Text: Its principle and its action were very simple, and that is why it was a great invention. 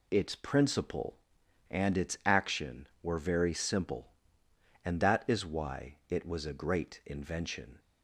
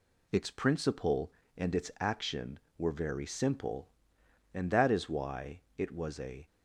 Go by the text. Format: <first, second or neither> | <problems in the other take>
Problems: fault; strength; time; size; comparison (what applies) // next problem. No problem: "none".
first | pauses between "why" and "it"; slight; at 5.5 s; 0.20 s long // stops before "great invention"; at 6.4 s